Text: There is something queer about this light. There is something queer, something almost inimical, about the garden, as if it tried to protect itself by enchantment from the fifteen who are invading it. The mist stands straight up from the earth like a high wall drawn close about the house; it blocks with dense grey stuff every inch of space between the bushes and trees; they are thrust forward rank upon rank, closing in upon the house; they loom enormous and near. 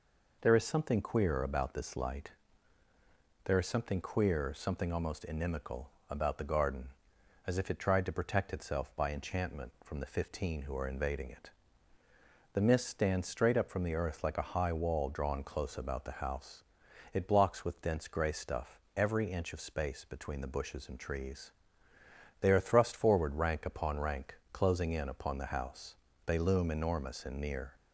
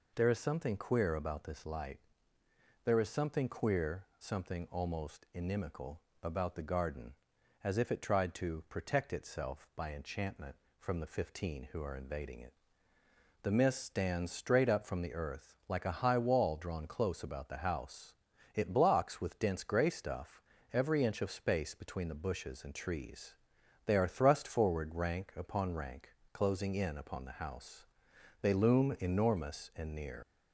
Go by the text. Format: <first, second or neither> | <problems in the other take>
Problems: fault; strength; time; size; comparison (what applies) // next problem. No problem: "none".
first | pauses between "stuff" and "every"; slight; at 20.4 s; 0.32 s long; slight in the first // leaves "near" unfinished; at 30.2 s; 100 ms